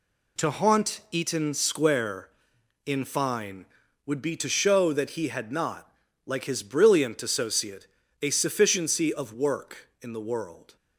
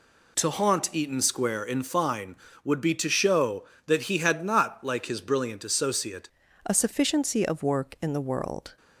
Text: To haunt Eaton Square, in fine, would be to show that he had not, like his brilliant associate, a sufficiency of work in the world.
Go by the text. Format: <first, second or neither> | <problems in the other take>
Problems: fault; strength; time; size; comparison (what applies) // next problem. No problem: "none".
first | changes voice at "a"; from 6.6 s on; 2.1 s long